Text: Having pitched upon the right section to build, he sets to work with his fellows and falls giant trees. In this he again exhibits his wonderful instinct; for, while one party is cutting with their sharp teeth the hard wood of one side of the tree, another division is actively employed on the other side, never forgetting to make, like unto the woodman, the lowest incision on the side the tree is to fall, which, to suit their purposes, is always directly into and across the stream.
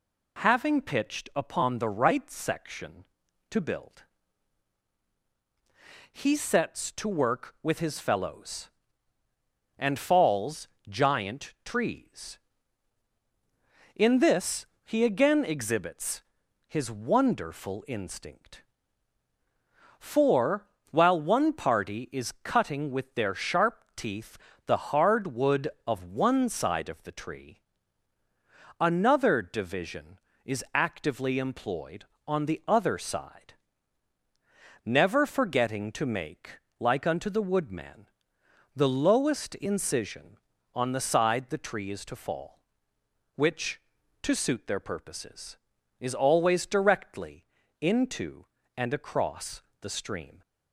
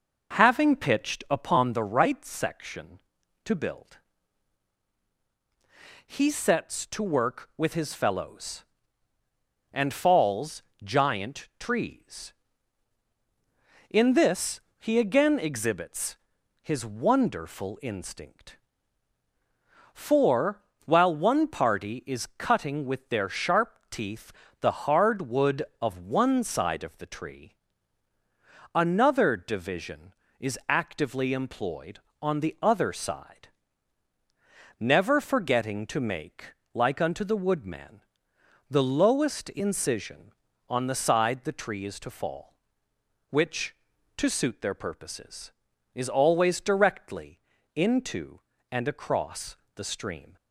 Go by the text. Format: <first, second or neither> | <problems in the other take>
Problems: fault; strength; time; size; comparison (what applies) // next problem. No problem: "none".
first | starts louder than the rest; noticeable; until 1.8 s; 5.5 dB // pauses between "falls" and "giant"; slight; at 10.6 s; 0.20 s long; slight in the first // pauses between "this" and "he"; slight; at 14.6 s; 0.18 s long; slight in the first // pauses between "exhibits" and "his"; noticeable; at 16.1 s; 0.46 s long; noticeable in the first // pauses between "teeth" and "the"; slight; at 24.3 s; 0.30 s long; slight in the first // pauses between "directly" and "into"; at 47.3 s; 0.38 s long; also in the first // pauses between "across" and "the"; slight; at 49.5 s; 0.20 s long; slight in the first